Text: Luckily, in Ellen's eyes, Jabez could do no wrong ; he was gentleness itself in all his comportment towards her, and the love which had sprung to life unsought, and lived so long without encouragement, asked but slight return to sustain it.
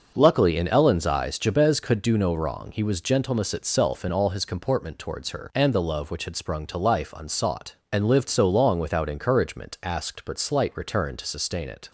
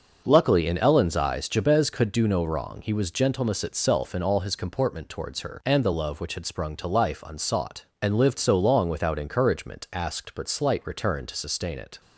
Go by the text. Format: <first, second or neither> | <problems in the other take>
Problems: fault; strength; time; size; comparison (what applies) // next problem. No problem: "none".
neither | starts louder than the rest; the same in both